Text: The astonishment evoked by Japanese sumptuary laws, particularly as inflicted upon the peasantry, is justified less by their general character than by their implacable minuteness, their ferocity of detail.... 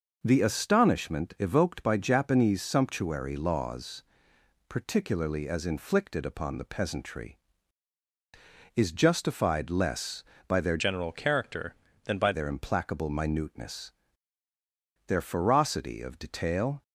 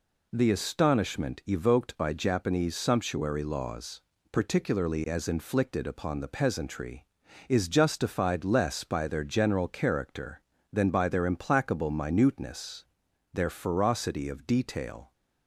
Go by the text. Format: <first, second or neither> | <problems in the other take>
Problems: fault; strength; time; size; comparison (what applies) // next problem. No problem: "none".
second | changes voice from "general" to "by"; from 10.7 to 12.3 s; 1.6 s long